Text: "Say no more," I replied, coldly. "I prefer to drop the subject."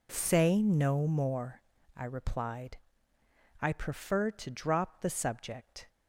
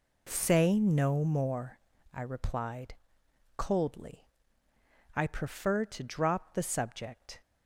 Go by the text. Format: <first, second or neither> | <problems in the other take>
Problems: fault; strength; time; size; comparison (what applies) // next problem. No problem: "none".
second | skips "coldly"; at 3.1 s